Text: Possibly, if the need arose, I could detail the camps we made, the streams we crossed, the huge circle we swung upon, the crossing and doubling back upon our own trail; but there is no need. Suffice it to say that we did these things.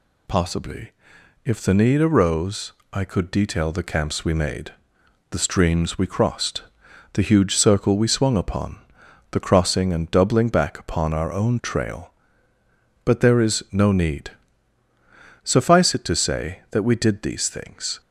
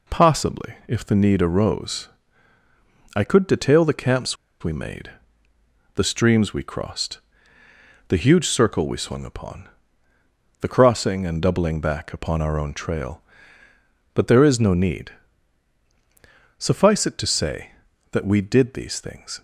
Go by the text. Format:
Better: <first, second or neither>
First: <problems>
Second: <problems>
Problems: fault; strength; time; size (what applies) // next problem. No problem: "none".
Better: first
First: none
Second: pauses between "camps" and "we"; slight; at 4.3 s; 0.27 s long